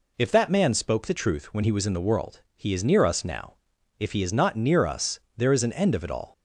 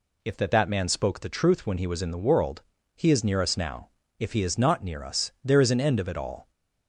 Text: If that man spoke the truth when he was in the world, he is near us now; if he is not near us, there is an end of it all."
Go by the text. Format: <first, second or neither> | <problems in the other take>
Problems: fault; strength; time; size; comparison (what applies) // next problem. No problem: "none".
first | says "that" twice; at 0.4 s